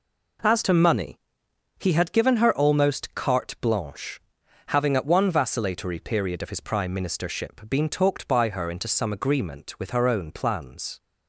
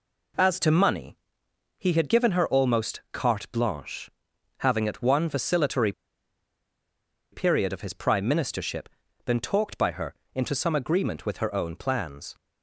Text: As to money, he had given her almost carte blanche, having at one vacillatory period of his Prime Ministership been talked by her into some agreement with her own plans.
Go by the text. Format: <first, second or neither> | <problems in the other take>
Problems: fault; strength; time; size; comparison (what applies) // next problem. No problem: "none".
first | pauses between "vacillatory" and "period"; strong; at 5.9 s; 1.3 s long // pauses between "Ministership" and "been"; at 8.8 s; 0.40 s long // pauses between "her" and "into"; slight; at 10.1 s; 0.22 s long